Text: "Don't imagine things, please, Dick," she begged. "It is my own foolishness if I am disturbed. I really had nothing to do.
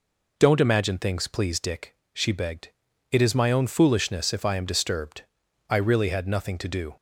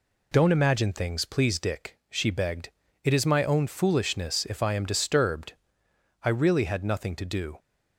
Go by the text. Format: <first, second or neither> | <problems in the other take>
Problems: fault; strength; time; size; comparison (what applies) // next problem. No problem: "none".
neither | none